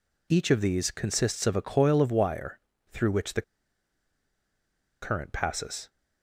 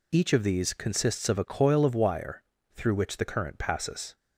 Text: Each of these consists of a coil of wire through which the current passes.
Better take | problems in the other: second | pauses between "wire" and "through"; slight; at 2.5 s; 0.34 s long; slight in the second // pauses between "the" and "current"; strong; at 3.4 s; 1.6 s long

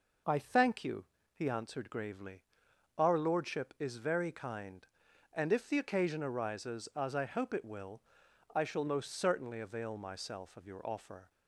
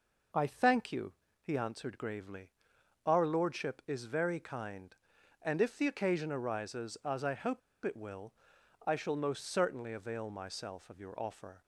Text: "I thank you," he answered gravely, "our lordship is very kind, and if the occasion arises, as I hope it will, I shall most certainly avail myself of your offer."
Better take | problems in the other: first | pauses between "hope" and "it"; slight; at 7.6 s; 0.24 s long

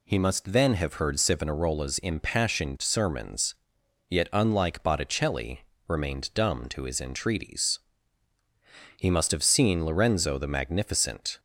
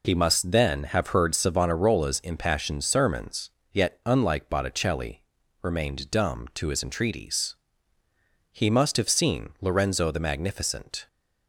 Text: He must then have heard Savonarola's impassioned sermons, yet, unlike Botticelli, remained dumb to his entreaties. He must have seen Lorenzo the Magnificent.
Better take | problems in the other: neither | none

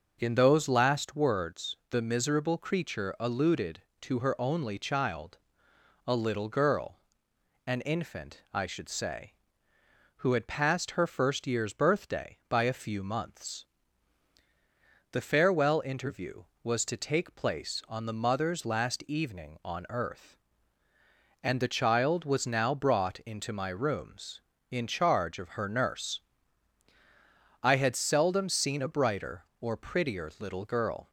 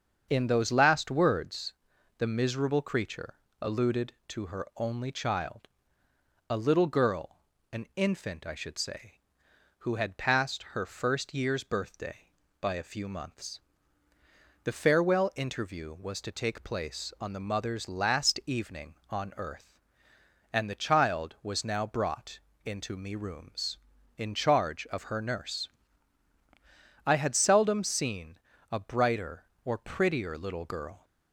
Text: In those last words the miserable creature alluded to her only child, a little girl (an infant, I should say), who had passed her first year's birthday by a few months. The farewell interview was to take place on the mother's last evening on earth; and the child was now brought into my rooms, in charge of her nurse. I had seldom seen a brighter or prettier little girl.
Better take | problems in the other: first | starts louder than the rest; until 1.3 s; 7 dB // pauses between "words" and "the"; noticeable; at 1.7 s; 0.46 s long // pauses between "creature" and "alluded"; slight; at 3.3 s; 0.28 s long // pauses between "brought" and "into"; slight; at 22.3 s; 0.28 s long // says "me" for "my"; at 22.9 s // pauses between "seen" and "a"; slight; at 28.3 s; 0.32 s long

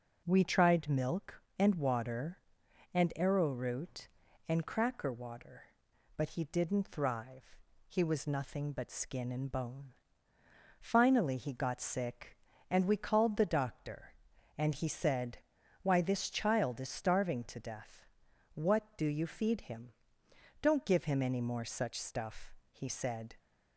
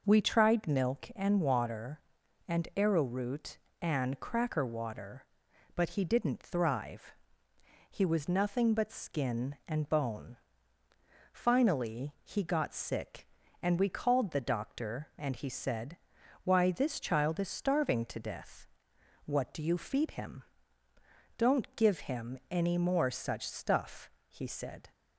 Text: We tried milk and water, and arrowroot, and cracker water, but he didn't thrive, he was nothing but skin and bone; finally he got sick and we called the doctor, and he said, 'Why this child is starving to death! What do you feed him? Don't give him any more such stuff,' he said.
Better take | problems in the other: neither | none

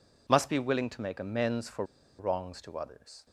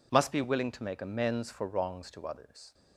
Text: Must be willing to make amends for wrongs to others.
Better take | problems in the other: second | pauses between "for" and "wrongs"; slight; at 1.8 s; 0.34 s long

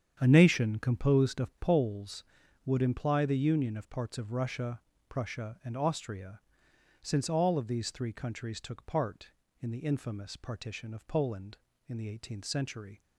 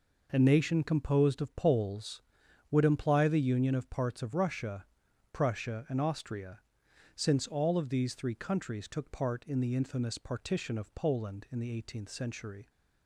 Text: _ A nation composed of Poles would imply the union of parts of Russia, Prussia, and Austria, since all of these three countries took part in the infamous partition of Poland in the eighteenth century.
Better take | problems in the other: second | starts louder than the rest; strong; until 1.8 s; 8 dB

